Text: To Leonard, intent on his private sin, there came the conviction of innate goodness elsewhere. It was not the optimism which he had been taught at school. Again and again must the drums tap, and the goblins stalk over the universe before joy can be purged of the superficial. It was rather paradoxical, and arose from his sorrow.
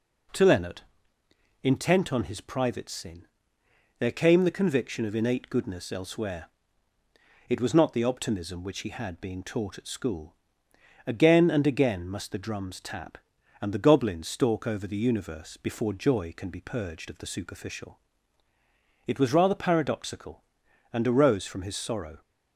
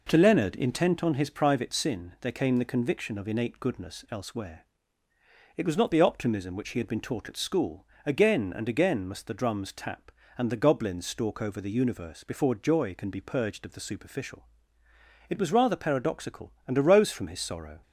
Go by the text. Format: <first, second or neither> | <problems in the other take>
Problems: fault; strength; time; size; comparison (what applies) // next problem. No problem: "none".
second | says "being" for "been"; at 9.1 s